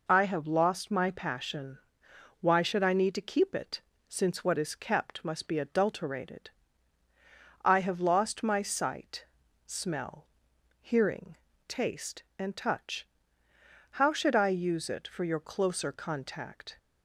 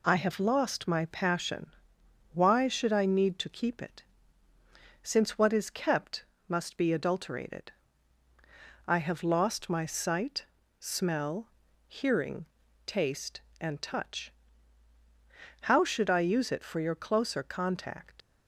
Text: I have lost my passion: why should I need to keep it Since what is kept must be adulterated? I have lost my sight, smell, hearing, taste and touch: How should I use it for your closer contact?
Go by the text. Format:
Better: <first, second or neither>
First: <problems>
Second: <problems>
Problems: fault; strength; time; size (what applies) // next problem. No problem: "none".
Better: first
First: pauses between "it" and "Since"; slight; at 3.8 s; 0.26 s long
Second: pauses between "it" and "Since"; noticeable; at 4.0 s; 0.98 s long // pauses between "kept" and "must"; slight; at 6.2 s; 0.22 s long // leaves "contact" unfinished; at 18.2 s; 70 ms